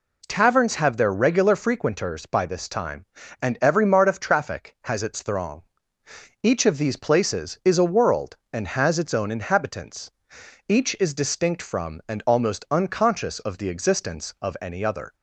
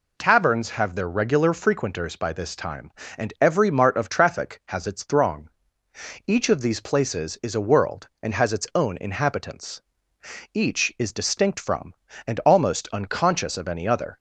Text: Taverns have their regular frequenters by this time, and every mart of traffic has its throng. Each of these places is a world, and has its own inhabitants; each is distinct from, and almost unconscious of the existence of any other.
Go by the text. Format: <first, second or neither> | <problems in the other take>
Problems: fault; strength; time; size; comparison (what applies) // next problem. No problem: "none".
first | skips "of the existence"; at 13.5 s